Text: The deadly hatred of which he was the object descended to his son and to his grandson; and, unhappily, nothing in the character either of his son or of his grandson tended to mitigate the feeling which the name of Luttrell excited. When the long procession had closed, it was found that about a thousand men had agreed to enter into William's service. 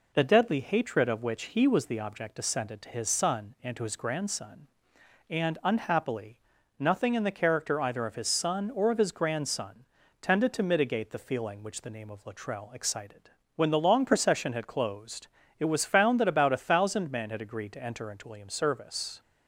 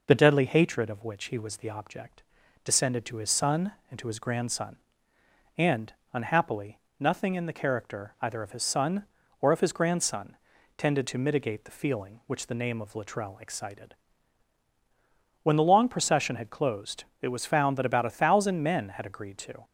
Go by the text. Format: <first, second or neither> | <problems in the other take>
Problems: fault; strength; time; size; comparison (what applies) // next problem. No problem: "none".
first | pauses between "object" and "descended"; at 2.2 s; 0.40 s long // pauses between "grandson" and "tended"; at 10.3 s; 0.40 s long; slight in the first // stops before "enter into William's service"; at 19.6 s